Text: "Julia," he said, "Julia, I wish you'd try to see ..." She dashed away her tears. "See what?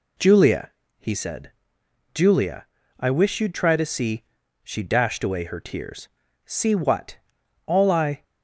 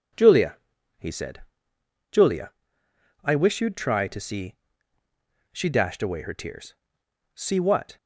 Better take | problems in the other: second | goes on to say "All I"; from 7.6 s on; 0.56 s long

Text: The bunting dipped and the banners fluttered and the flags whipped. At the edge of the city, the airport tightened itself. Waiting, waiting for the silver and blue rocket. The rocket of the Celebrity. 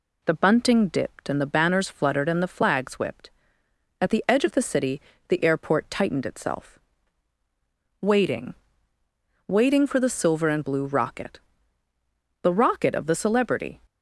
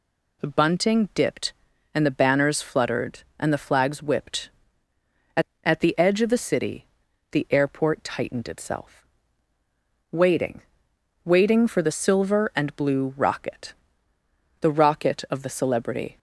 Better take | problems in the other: first | says "At" twice; at 5.6 s

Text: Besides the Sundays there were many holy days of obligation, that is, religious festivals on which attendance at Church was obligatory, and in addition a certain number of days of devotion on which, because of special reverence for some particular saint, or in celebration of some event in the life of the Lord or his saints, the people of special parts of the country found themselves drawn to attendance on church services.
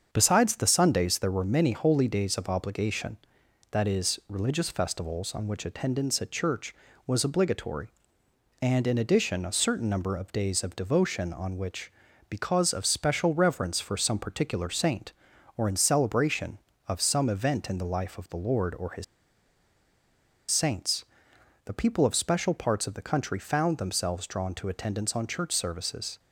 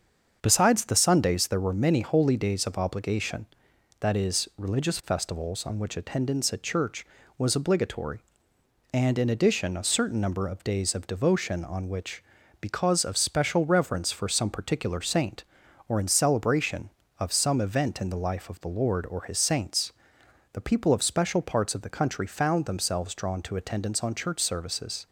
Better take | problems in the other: second | starts louder than the rest; until 1.1 s; 7 dB; also in the second // pauses between "his" and "saints"; strong; at 19.0 s; 1.4 s long

